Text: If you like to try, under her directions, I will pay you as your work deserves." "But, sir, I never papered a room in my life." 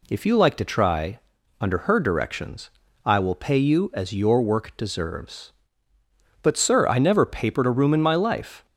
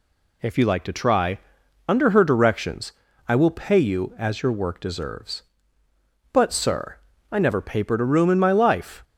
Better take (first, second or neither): neither